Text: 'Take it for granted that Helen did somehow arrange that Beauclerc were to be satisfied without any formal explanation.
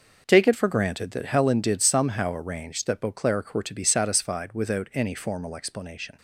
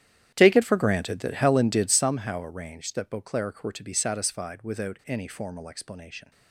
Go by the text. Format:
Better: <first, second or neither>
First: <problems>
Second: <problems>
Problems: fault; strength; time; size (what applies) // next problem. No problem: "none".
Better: first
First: none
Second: starts louder than the rest; strong; until 2.2 s; 10.5 dB